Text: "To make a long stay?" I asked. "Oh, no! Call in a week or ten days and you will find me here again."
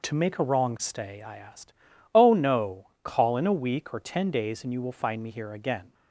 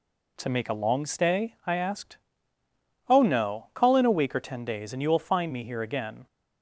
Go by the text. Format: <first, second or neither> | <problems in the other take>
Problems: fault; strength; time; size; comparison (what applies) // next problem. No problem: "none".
second | says "wrong" for "long"; at 0.4 s